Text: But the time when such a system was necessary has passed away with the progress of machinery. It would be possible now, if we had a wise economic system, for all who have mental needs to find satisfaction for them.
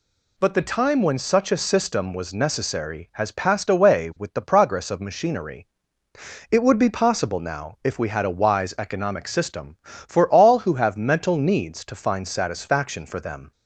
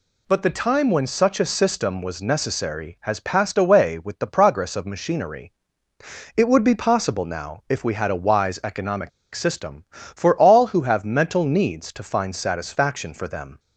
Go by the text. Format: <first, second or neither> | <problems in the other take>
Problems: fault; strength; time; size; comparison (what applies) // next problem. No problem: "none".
first | pauses between "economic" and "system"; slight; at 9.0 s; 0.25 s long